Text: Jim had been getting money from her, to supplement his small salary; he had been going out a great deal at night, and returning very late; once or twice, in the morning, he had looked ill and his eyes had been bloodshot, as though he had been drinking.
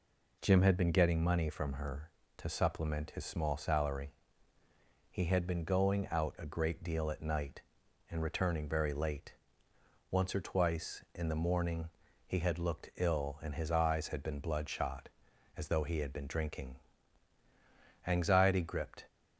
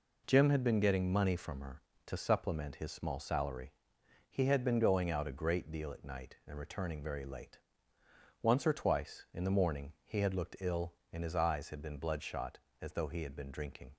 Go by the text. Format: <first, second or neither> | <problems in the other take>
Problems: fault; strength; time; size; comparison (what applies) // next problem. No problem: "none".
second | goes on to say "Anxiety gripped"; noticeable; from 18.0 s on; 1.0 s long